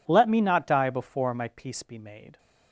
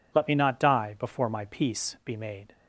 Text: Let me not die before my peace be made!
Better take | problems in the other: neither | none

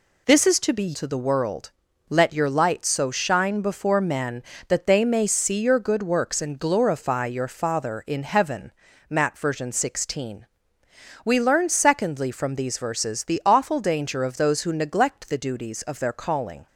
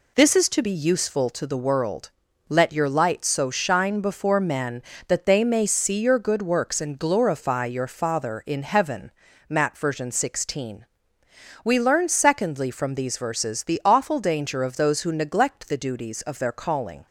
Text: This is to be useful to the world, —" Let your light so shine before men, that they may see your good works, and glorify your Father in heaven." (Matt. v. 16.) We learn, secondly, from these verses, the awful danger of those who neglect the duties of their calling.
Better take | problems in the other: second | skips "useful"; at 0.9 s

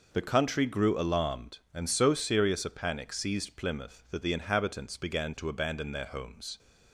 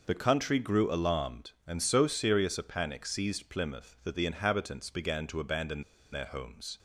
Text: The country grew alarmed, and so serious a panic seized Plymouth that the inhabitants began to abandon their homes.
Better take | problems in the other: first | pauses between "abandon" and "their"; slight; at 5.8 s; 0.30 s long

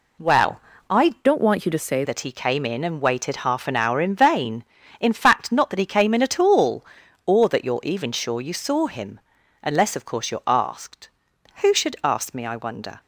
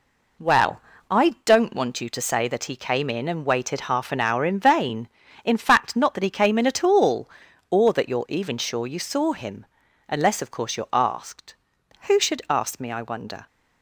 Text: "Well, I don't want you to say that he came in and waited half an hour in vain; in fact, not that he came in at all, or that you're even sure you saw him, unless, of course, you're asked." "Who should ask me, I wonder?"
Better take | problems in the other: second | changes voice from "don't" to "say"; from 1.2 to 2.0 s; 0.8 s long

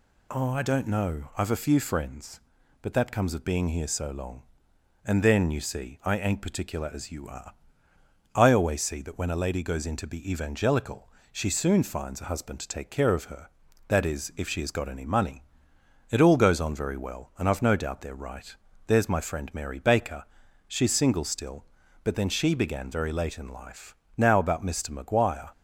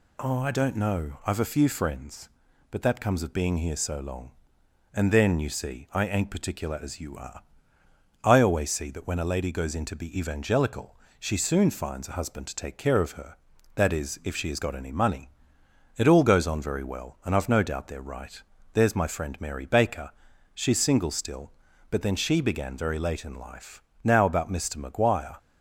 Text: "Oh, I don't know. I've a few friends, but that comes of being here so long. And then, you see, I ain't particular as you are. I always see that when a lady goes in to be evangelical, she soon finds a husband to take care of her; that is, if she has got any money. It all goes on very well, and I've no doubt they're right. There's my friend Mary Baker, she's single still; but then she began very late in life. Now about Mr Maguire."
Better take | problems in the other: neither | none

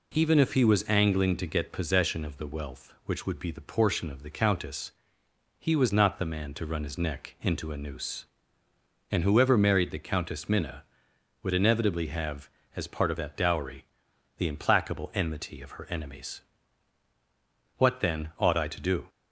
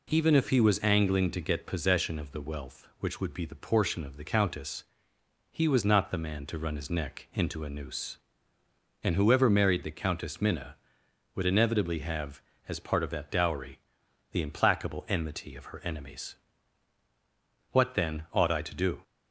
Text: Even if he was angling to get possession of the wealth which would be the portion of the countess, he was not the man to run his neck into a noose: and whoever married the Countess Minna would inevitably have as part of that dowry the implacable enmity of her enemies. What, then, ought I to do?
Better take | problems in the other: neither | pauses between "dowry" and "the"; noticeable; the same in both

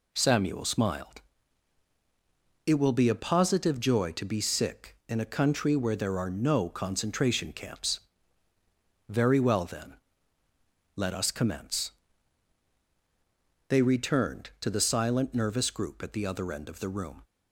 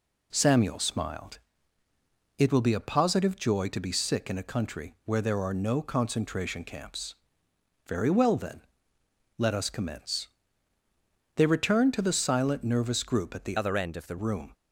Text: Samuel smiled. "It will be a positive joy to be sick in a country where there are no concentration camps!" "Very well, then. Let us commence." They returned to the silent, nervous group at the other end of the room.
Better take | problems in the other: first | changes voice from "other" to "the"; from 13.5 to 14.1 s; 0.6 s long

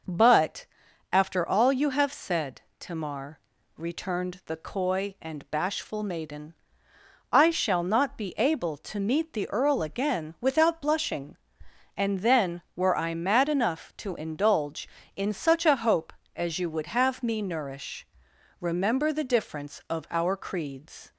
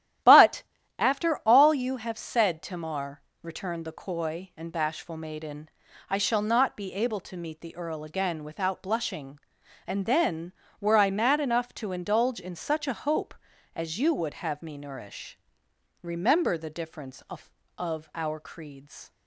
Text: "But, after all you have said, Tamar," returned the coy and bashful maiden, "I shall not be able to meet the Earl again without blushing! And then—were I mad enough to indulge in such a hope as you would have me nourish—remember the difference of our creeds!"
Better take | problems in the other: first | starts louder than the rest; strong; until 1.6 s; 12.5 dB // says "of" twice; at 17.7 s

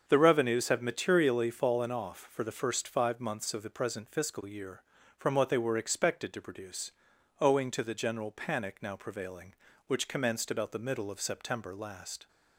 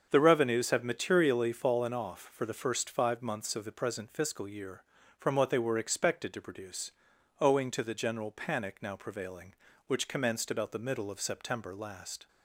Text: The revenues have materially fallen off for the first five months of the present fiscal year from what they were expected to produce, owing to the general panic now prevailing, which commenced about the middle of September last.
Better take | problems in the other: neither | starts louder than the rest; the same in both

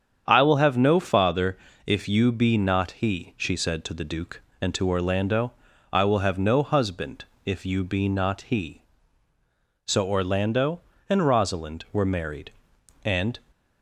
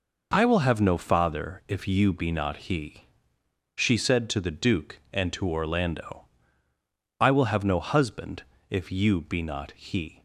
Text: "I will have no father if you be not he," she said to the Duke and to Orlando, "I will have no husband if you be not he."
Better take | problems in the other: second | starts louder than the rest; strong; until 1.2 s; 8 dB // pauses between "father" and "if"; slight; at 1.5 s; 0.30 s long // pauses between "husband" and "if"; slight; at 7.2 s; 0.20 s long; slight in the second // goes on to say "So Orlando and Rosalind were married and"; strong; from 9.8 s on; 3.5 s long

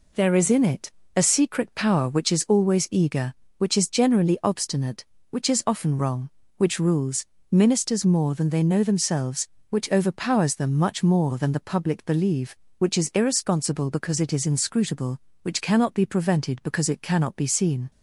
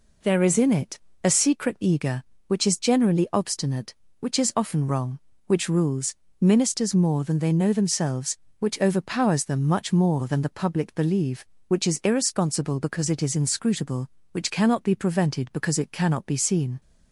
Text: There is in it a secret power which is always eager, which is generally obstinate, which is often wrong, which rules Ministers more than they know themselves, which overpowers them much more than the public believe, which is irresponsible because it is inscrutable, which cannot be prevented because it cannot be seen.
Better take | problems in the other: first | pauses between "it" and "a"; slight; at 0.9 s; 0.26 s long; slight in the first // skips "power which is always"; at 1.8 s // pauses between "rules" and "Ministers"; slight; at 6.1 s; 0.26 s long; slight in the first

